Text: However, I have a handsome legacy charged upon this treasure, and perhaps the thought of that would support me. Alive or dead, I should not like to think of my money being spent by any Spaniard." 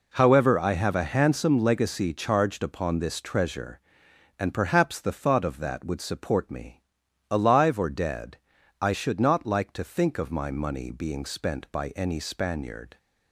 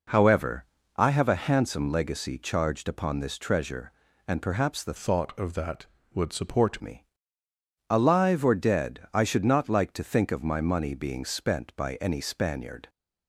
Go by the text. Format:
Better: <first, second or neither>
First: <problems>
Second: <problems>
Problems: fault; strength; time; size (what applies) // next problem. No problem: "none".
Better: first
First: none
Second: changes voice from "thought" to "support"; from 4.9 to 6.8 s; 1.9 s long